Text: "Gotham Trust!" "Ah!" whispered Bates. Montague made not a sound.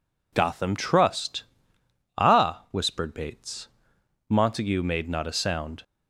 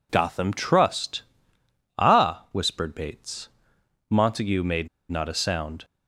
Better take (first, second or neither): first